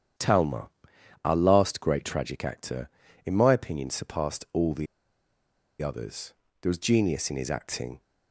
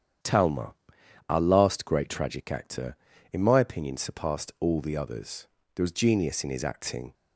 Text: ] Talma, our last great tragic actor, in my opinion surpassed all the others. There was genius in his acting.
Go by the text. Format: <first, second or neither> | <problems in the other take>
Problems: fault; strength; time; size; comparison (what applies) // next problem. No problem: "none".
second | starts louder than the rest; strong; until 1.7 s; 9 dB; strong in the second // pauses between "the" and "others"; noticeable; at 4.8 s; 0.95 s long